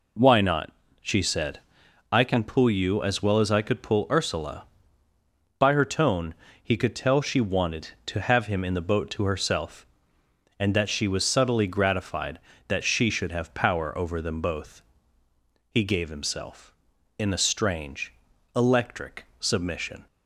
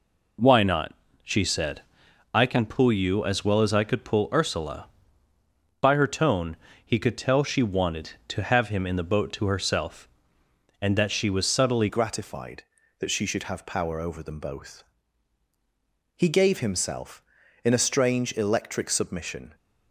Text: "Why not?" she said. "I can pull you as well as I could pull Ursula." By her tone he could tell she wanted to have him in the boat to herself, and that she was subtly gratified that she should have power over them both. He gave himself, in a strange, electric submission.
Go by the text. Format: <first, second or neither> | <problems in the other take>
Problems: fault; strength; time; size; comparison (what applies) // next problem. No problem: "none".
first | pauses between "tone" and "he"; slight; at 6.5 s; 0.30 s long; slight in the first // changes voice at "gratified"; from 11.8 s on; 7.7 s long